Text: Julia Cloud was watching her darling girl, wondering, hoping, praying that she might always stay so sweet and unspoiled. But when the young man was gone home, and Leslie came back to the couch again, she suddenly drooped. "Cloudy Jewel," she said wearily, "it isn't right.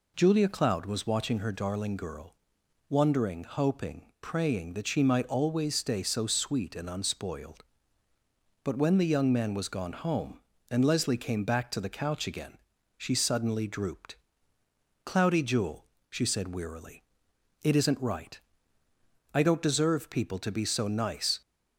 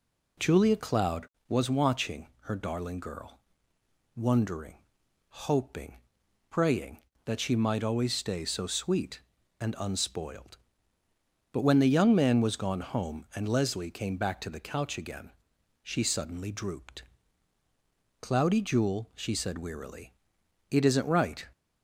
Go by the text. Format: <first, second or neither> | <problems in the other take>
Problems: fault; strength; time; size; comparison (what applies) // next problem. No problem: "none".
second | goes on to say "I don't deserve people to be so nice"; strong; from 19.3 s on; 2.0 s long